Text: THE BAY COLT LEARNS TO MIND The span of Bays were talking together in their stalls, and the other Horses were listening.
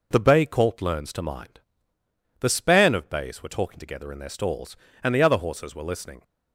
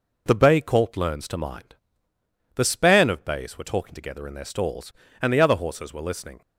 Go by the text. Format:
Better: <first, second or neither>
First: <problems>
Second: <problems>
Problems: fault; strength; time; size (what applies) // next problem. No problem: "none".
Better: neither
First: pauses between "MIND" and "The"; noticeable; at 1.5 s; 0.80 s long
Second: pauses between "MIND" and "The"; noticeable; at 1.7 s; 0.80 s long